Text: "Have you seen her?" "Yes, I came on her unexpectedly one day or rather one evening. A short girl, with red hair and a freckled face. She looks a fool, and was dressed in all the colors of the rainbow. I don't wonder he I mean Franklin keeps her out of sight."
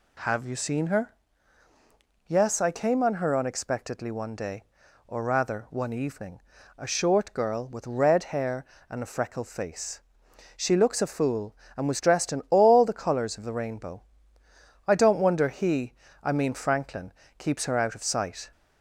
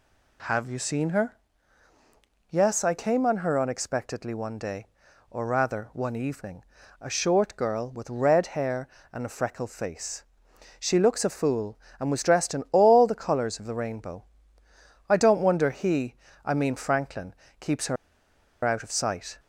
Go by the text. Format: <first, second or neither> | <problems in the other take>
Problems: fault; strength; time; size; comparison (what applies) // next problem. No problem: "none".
first | pauses between "he" and "I"; slight; at 16.1 s; 0.28 s long; slight in the first // pauses between "Franklin" and "keeps"; slight; at 17.3 s; 0.24 s long; slight in the first // pauses between "her" and "out"; noticeable; at 17.9 s; 0.69 s long